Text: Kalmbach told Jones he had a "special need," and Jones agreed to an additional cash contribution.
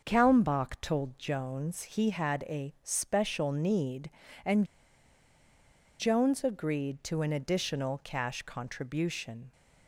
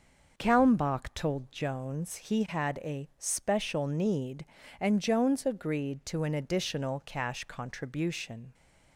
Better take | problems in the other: second | starts louder than the rest; until 1.0 s; 6 dB; also in the second // pauses between "and" and "Jones"; strong; at 4.6 s; 1.3 s long

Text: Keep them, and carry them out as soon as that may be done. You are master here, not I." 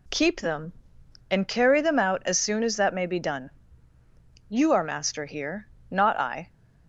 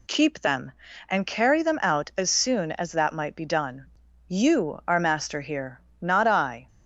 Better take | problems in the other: first | says "might" for "may"; at 3.1 s

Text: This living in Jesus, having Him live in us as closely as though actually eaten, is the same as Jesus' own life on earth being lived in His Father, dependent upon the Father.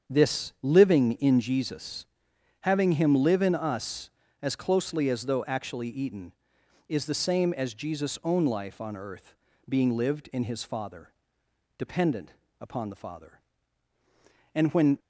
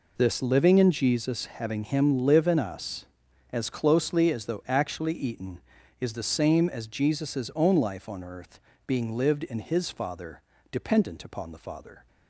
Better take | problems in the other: second | starts louder than the rest; strong; until 1.1 s; 7.5 dB // pauses between "earth" and "being"; slight; at 9.3 s; 0.34 s long; slight in the second // pauses between "dependent" and "upon"; slight; at 12.3 s; 0.28 s long // goes on to say "And when"; slight; from 14.5 s on; 0.44 s long

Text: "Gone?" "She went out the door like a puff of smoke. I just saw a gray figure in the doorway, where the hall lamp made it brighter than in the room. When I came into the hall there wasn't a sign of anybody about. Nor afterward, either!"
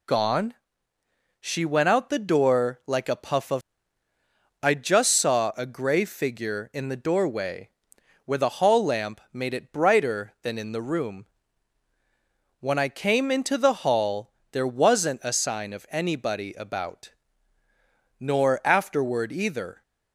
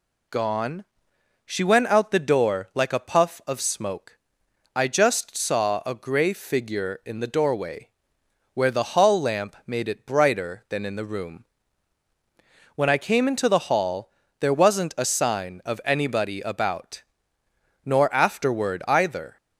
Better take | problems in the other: second | skips "smoke"; at 4.1 s // pauses between "hall" and "there"; slight; at 14.3 s; 0.20 s long; slight in the second

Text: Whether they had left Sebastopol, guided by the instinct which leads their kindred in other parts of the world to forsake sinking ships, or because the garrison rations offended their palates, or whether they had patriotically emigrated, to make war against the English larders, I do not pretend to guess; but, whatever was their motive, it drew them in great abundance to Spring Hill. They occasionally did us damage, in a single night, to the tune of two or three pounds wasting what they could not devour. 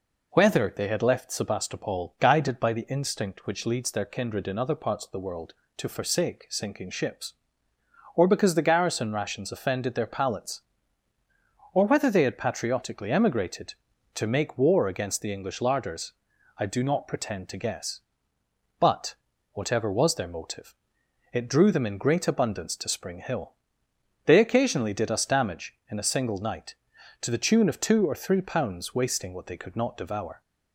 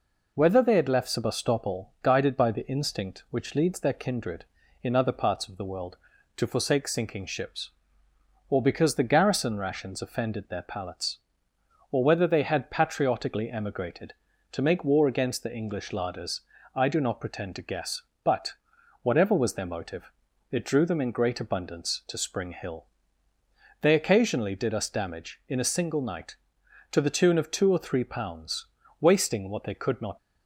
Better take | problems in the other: first | pauses between "pounds" and "wasting"; slight; at 28.6 s; 0.32 s long // stops before "devour"; at 30.1 s

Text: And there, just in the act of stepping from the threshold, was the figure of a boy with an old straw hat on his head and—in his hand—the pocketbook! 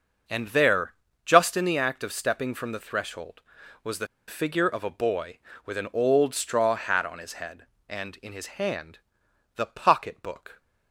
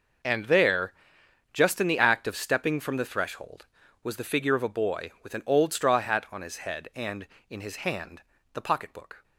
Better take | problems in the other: second | starts louder than the rest; until 1.5 s; 6 dB // pauses between "the" and "figure"; slight; at 4.0 s; 0.22 s long

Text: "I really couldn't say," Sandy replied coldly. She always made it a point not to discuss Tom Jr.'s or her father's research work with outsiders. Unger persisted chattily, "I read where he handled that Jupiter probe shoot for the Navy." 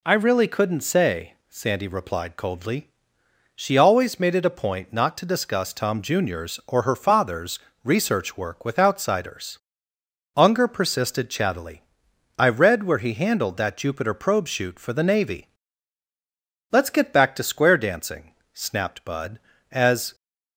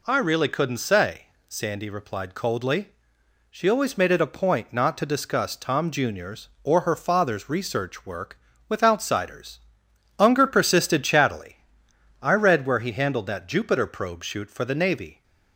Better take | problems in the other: second | pauses between "father's" and "research"; slight; at 7.5 s; 0.26 s long // goes on to say "Let's get back to square dancing snapped Bud As"; strong; from 16.7 s on; 3.4 s long

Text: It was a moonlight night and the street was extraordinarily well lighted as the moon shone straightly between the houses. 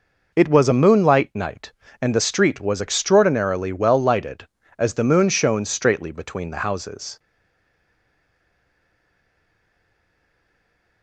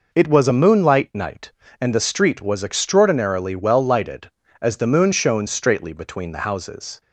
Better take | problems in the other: second | stays silent after the last word; strong; from 7.1 s on; 3.9 s long

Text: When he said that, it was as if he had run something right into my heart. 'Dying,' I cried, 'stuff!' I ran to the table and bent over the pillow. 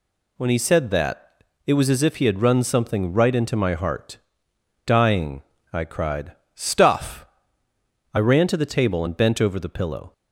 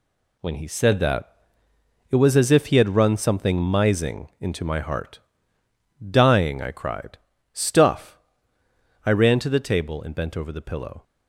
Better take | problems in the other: first | says "mising" for "right"; at 3.5 s

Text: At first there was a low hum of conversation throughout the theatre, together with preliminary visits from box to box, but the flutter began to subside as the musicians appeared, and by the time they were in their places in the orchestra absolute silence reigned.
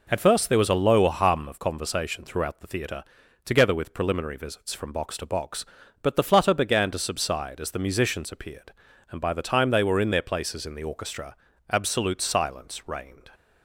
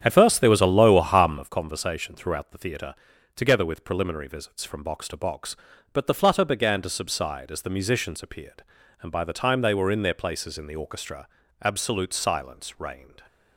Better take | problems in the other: first | starts louder than the rest; strong; until 1.5 s; 9 dB // pauses between "orchestra" and "absolute"; slight; at 11.2 s; 0.34 s long; slight in the first

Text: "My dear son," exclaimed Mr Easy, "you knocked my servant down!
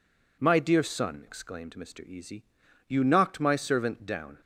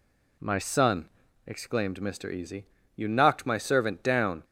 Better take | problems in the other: first | skips "dear"; at 0.5 s

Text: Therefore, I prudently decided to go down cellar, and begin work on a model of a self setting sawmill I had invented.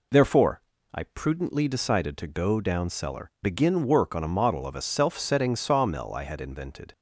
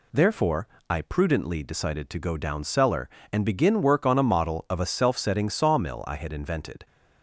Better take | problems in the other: second | skips "and"; at 3.3 s

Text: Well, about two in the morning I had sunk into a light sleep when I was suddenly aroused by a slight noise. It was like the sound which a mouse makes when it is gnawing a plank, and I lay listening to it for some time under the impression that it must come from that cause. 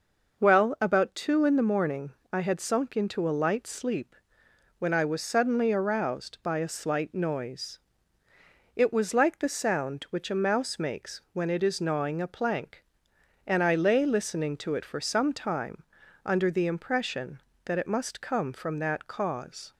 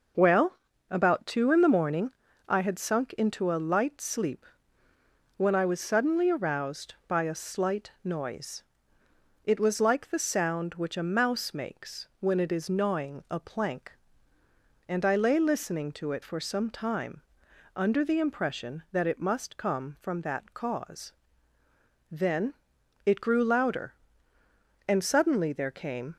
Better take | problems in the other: first | pauses between "morning" and "I"; at 2.0 s; 0.38 s long; slight in the first // pauses between "sleep" and "when"; noticeable; at 4.4 s; 0.90 s long; noticeable in the first // pauses between "time" and "under"; noticeable; at 17.1 s; 0.56 s long; also in the first // goes on to say "Then it grew louder and suddenly there came"; strong; from 22.0 s on; 4.0 s long

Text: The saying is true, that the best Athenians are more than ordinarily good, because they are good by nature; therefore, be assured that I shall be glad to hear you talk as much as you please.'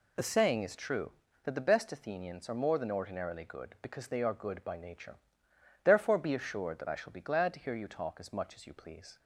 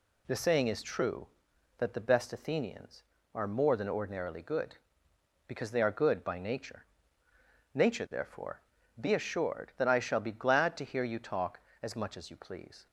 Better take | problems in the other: first | says "nature" twice; at 7.7 s

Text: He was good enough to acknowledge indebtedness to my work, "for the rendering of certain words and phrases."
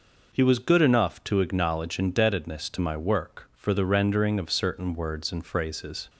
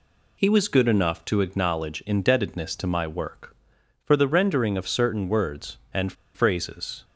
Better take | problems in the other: first | pauses between "and" and "phrases"; slight; at 6.1 s; 0.21 s long

